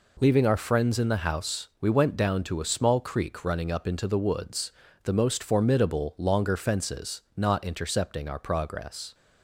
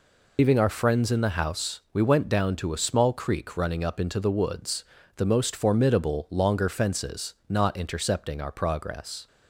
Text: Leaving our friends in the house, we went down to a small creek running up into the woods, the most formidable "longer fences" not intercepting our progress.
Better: first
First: none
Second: loses the start of "Leaving"; at 0.3 s; 95 ms

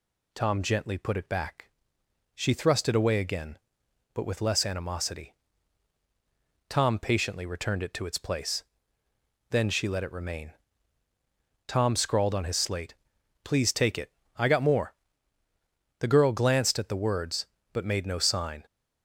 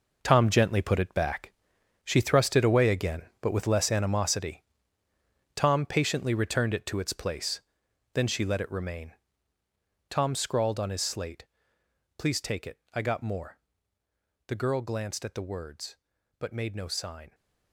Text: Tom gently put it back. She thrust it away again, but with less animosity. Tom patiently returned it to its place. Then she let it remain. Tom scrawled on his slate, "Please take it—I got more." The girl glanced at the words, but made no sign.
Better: first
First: none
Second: gets quieter; strong; throughout; 11 dB

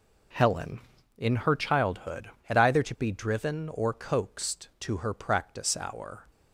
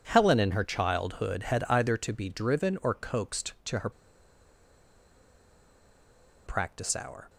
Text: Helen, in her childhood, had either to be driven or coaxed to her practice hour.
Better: first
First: none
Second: pauses between "her" and "practice"; strong; at 3.8 s; 2.5 s long

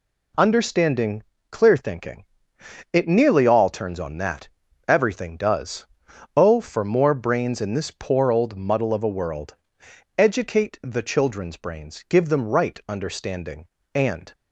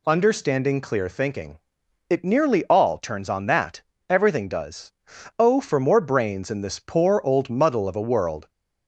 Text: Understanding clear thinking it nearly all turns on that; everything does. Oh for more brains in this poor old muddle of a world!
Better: second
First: pauses between "Understanding" and "clear"; slight; at 1.2 s; 0.30 s long // pauses between "thinking" and "it"; noticeable; at 2.2 s; 0.68 s long // goes on to say "Educate the children's brains give them right understanding and"; strong; from 10.1 s on; 4.1 s long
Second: pauses between "thinking" and "it"; noticeable; at 1.5 s; 0.50 s long

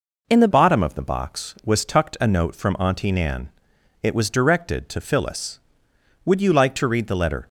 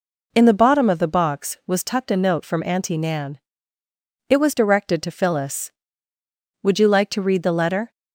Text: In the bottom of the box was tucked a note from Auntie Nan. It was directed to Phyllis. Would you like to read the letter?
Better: second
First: changes voice at "bottom"; from 0.5 s on; 6.9 s long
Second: none

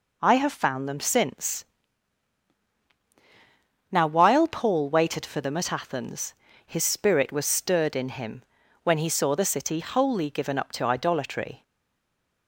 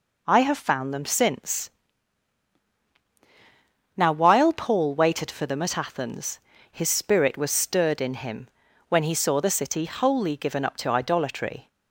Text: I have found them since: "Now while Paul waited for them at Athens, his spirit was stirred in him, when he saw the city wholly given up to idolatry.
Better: second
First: stays silent after the last word; slight; from 11.6 s on; 0.8 s long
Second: none

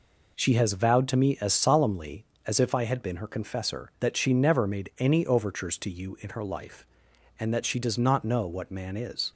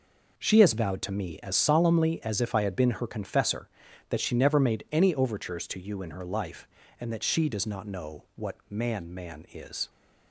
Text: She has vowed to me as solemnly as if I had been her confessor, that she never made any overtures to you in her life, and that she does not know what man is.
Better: first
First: none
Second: says "man" twice; at 9.1 s

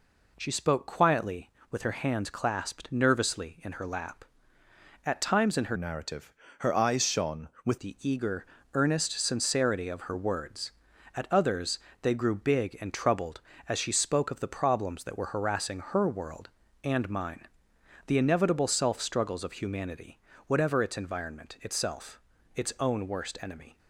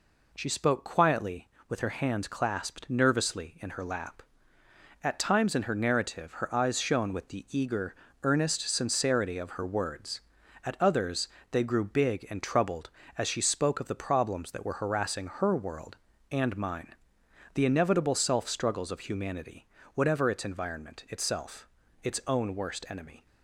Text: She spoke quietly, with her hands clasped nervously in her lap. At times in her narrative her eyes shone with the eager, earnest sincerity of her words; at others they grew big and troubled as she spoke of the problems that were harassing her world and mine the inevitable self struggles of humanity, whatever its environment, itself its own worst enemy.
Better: second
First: changes voice from "narrative" to "with"; from 5.7 to 7.7 s; 2.0 s long // pauses between "narrative" and "her"; slight; at 6.3 s; 0.24 s long // pauses between "others" and "they"; slight; at 11.7 s; 0.24 s long // pauses between "mine" and "the"; noticeable; at 17.4 s; 0.60 s long // pauses between "itself" and "its"; slight; at 22.1 s; 0.36 s long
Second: pauses between "others" and "they"; slight; at 11.2 s; 0.24 s long // pauses between "mine" and "the"; noticeable; at 16.9 s; 0.60 s long // pauses between "itself" and "its"; slight; at 21.6 s; 0.36 s long

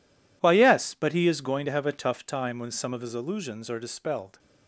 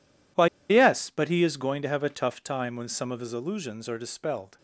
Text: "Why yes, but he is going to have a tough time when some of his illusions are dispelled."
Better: first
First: none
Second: pauses between "Why" and "yes"; slight; at 0.4 s; 0.23 s long

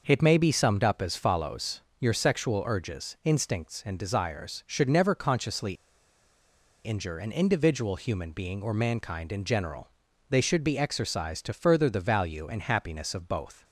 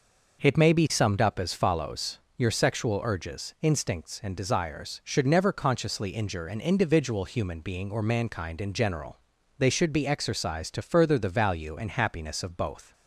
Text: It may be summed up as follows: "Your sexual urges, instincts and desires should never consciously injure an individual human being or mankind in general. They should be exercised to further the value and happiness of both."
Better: second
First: pauses between "consciously" and "injure"; at 5.7 s; 1.1 s long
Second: none

